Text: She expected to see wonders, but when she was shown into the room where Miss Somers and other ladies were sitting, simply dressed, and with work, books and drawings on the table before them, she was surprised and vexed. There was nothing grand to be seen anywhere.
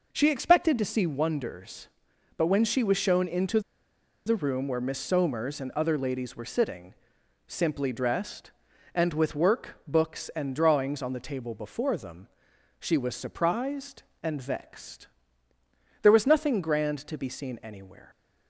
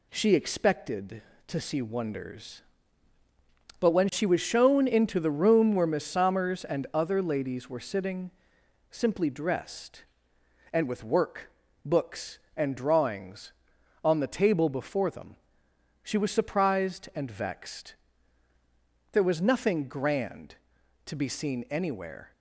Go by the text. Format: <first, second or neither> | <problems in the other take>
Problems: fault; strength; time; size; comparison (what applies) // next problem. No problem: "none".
second | pauses between "into" and "the"; noticeable; at 3.6 s; 0.65 s long